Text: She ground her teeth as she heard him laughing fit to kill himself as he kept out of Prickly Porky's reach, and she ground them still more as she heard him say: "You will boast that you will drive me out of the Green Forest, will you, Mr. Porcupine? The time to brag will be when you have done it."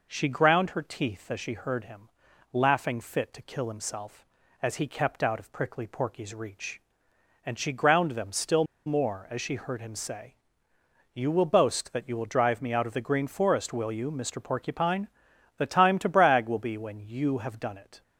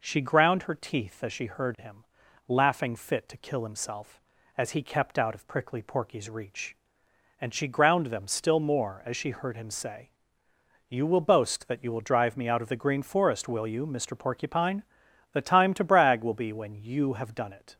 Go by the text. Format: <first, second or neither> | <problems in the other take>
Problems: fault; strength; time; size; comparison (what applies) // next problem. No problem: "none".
second | pauses between "him" and "laughing"; noticeable; at 2.0 s; 0.46 s long; noticeable in the second // pauses between "still" and "more"; slight; at 8.6 s; 0.22 s long